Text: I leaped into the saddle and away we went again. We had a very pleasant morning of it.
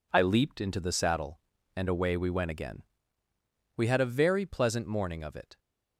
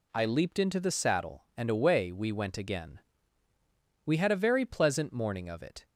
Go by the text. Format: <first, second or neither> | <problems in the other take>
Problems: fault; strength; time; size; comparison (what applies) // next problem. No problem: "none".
neither | none